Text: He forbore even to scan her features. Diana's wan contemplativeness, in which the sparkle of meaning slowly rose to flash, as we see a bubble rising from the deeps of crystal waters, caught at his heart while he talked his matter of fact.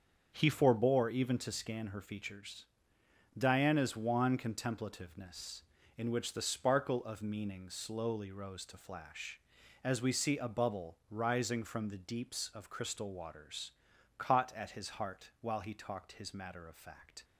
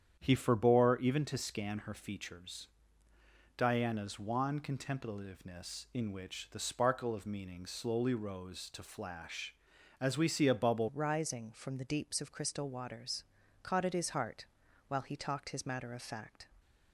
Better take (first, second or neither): first